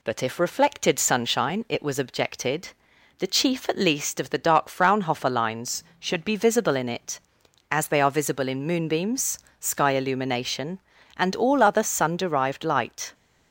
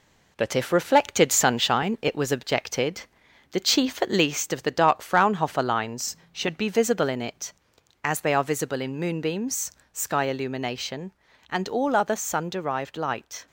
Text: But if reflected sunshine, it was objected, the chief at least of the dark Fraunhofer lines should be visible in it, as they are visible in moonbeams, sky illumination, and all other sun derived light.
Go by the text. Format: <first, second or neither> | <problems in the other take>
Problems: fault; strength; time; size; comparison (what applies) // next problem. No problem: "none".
first | gets quieter; noticeable; throughout; 4.5 dB